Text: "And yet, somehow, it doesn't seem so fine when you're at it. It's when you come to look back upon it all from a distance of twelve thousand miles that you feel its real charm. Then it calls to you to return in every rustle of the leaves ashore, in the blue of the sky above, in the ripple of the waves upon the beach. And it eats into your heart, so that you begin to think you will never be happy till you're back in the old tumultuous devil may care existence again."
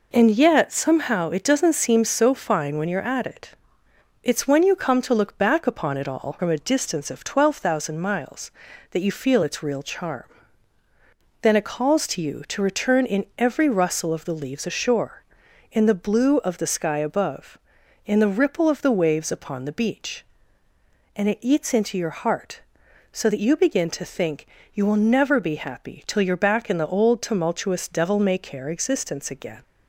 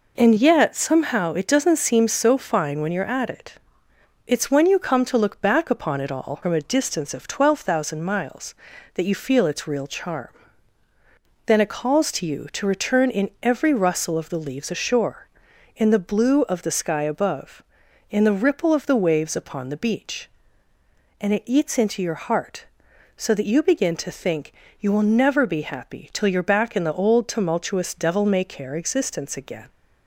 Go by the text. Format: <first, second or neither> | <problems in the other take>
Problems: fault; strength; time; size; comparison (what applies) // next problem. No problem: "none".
neither | pauses between "think" and "you"; slight; the same in both